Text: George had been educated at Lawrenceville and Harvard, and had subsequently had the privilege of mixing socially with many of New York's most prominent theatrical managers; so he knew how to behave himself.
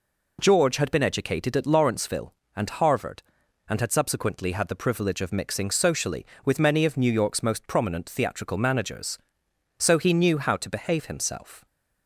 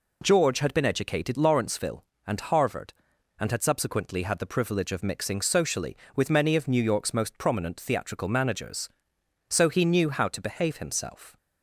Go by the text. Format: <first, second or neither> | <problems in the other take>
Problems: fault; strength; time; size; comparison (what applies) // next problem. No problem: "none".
first | skips "at"; at 1.3 s